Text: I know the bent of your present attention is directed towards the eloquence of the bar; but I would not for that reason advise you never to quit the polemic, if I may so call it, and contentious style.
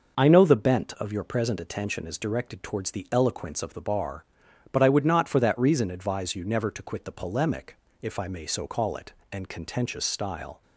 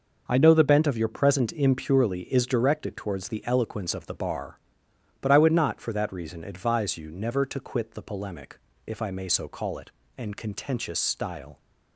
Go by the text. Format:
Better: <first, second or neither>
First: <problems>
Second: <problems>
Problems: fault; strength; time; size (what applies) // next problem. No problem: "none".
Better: first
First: none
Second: says "impurely" for "attention"; at 1.5 s